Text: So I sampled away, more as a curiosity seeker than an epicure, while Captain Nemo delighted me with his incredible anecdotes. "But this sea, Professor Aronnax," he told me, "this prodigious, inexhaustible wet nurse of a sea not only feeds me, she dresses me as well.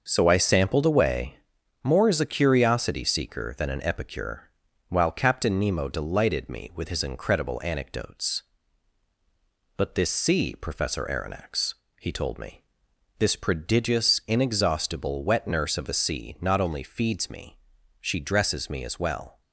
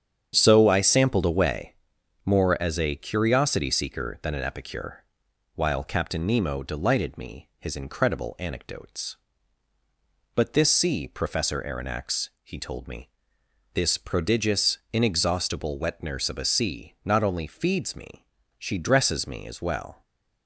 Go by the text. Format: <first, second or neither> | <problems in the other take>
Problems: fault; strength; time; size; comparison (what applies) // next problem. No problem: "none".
first | starts louder than the rest; strong; until 1.3 s; 8.5 dB; noticeable in the first // skips "with"; at 7.5 s // stays silent after the last word; slight; from 19.9 s on; 0.5 s long